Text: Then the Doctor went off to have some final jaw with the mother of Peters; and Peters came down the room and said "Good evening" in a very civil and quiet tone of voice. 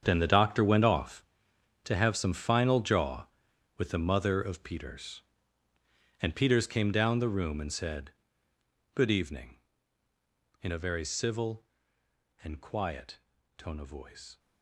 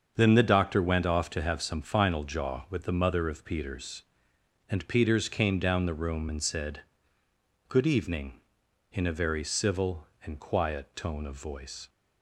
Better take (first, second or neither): second